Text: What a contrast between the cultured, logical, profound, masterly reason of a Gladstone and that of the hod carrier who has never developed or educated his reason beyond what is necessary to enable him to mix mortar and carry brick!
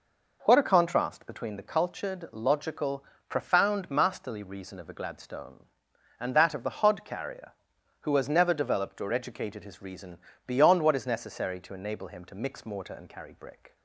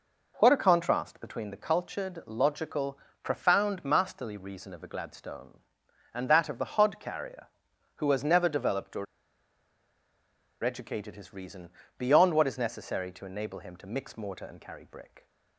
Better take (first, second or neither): first